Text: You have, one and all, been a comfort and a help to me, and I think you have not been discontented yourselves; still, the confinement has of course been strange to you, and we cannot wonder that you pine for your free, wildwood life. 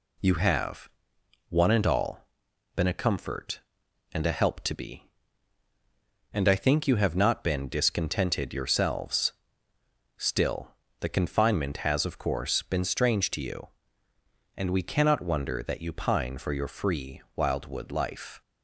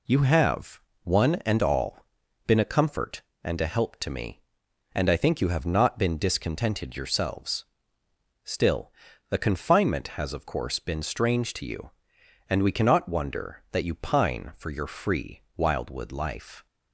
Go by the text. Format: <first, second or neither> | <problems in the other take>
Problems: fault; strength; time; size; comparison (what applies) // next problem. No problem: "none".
second | says "be" for "me"; at 4.7 s